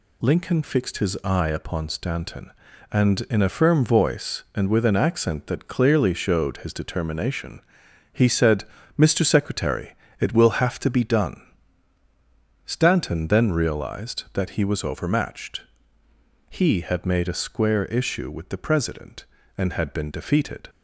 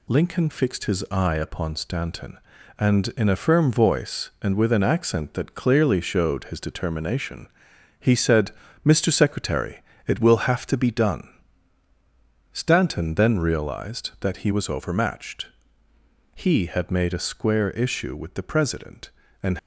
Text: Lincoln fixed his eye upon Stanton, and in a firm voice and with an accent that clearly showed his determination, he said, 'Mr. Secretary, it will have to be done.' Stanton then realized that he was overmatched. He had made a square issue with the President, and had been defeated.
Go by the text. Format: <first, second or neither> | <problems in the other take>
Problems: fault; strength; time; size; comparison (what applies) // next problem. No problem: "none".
first | stops before "had been defeated"; at 19.5 s